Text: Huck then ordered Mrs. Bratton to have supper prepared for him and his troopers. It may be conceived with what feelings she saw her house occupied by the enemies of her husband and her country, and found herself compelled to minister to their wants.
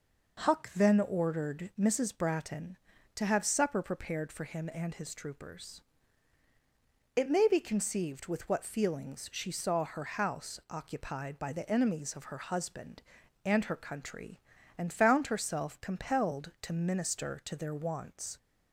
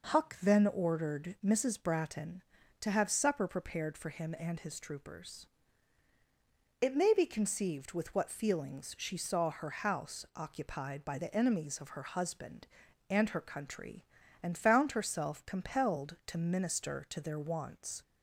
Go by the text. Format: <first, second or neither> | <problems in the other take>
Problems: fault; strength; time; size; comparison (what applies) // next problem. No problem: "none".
neither | none